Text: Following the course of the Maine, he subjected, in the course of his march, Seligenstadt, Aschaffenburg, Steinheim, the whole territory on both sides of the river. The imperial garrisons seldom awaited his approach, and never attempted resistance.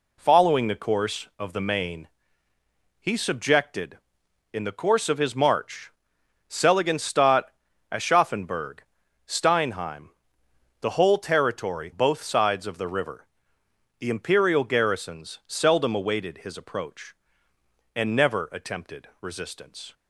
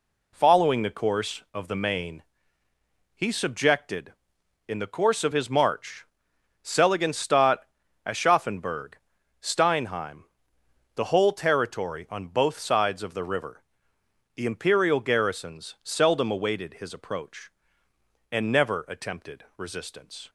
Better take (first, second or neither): second